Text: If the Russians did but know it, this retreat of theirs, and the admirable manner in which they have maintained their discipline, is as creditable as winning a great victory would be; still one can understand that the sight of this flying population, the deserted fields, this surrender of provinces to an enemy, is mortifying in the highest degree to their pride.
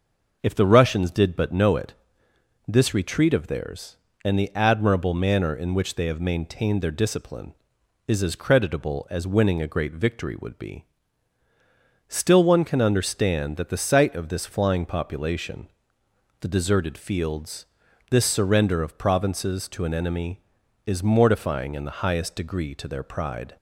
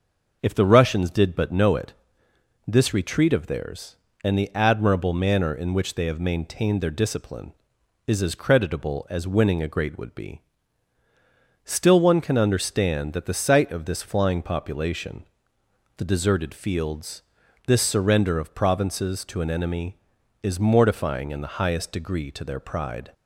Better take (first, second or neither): first